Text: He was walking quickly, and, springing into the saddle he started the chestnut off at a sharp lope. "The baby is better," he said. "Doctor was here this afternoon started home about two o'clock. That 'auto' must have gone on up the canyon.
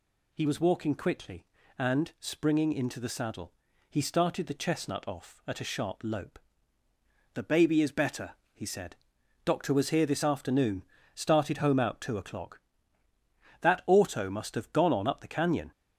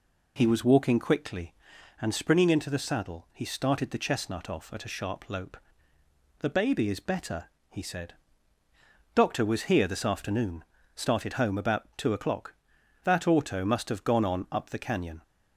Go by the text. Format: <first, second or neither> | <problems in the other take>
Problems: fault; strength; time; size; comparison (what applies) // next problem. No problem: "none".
second | pauses between "saddle" and "he"; slight; at 3.5 s; 0.36 s long // pauses between "afternoon" and "started"; slight; at 10.8 s; 0.32 s long; slight in the second // says "out" for "about"; at 11.7 s